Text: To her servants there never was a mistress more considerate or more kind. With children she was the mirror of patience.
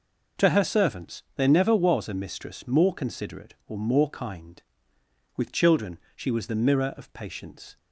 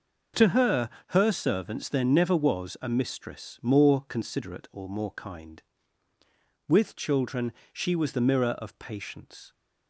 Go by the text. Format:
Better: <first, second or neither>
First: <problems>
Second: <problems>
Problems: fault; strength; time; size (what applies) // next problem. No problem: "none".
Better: first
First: pauses between "children" and "she"; slight; at 5.9 s; 0.16 s long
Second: says "her" twice; at 1.0 s // pauses between "children" and "she"; slight; at 7.5 s; 0.18 s long